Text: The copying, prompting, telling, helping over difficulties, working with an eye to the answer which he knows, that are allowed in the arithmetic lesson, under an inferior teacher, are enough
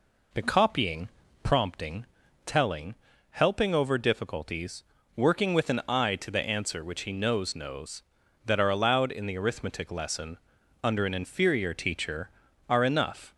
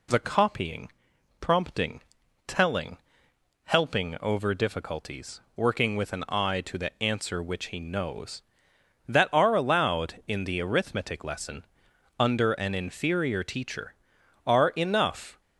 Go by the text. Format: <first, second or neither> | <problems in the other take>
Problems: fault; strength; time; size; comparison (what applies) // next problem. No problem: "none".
second | says "knows" twice; at 7.5 s